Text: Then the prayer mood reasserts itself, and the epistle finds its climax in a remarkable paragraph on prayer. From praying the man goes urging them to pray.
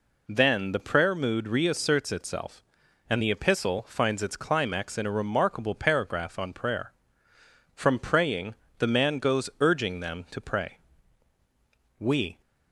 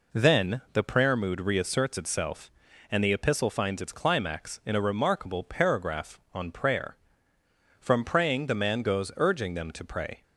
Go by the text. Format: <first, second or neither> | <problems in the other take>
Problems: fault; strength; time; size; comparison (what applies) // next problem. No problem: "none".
second | pauses between "praying" and "the"; slight; at 8.5 s; 0.24 s long // goes on to say "We"; slight; from 11.9 s on; 0.42 s long